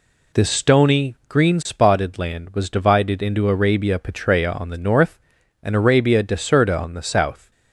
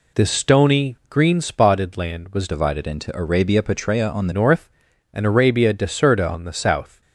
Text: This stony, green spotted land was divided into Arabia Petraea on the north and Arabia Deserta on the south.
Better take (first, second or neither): first